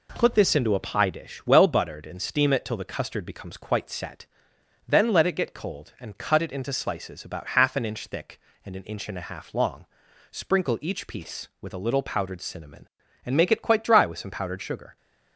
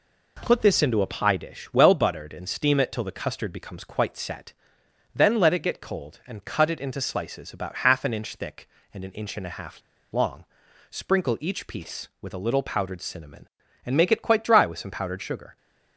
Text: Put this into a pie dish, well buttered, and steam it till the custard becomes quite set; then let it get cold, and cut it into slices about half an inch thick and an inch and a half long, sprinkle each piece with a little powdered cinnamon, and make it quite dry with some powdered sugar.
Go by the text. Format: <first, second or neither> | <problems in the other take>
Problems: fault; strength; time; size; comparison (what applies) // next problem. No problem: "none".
first | pauses between "half" and "long"; slight; at 9.8 s; 0.31 s long